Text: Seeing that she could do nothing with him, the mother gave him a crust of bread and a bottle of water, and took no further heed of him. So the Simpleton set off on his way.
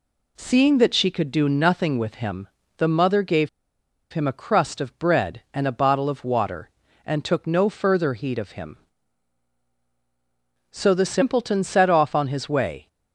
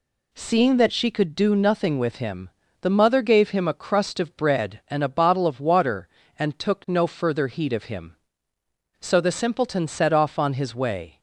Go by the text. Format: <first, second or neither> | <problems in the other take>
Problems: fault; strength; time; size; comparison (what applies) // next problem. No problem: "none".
second | pauses between "gave" and "him"; noticeable; at 3.4 s; 0.64 s long